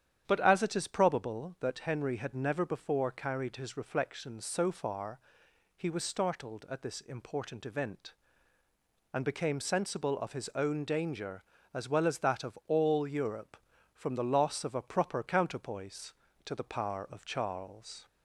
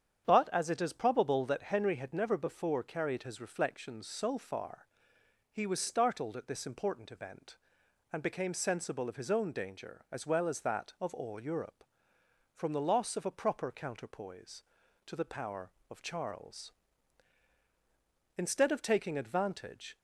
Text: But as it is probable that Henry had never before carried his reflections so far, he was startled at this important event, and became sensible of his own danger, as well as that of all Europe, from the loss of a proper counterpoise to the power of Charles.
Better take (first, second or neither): first